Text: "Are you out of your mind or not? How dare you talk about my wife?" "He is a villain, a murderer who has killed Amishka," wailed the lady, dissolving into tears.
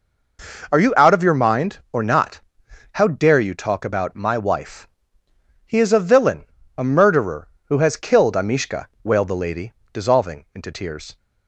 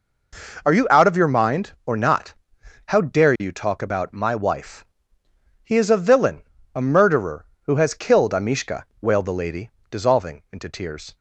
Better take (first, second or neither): neither